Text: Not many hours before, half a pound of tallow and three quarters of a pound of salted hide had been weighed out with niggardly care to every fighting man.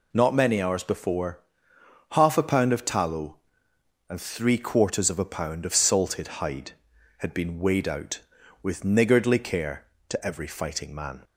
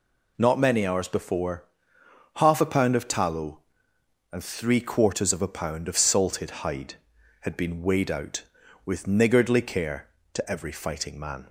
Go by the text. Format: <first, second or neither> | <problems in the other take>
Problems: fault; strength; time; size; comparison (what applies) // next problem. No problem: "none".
neither | none